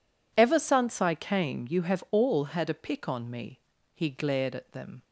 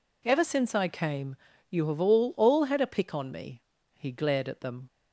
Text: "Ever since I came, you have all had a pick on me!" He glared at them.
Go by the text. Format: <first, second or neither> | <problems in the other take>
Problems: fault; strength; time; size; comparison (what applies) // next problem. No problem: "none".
first | says "all" twice; at 2.3 s